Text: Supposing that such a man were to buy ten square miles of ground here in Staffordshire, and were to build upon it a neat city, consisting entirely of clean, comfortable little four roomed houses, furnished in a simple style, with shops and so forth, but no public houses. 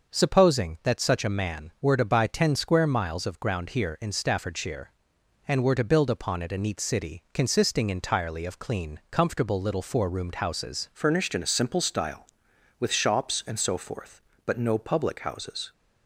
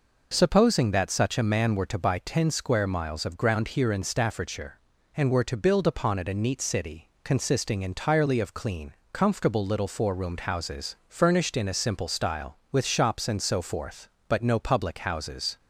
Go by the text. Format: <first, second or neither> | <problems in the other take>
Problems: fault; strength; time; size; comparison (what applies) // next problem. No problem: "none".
second | starts louder than the rest; until 1.1 s; 6.5 dB // changes voice at "furnished"; from 10.9 s on; 4.8 s long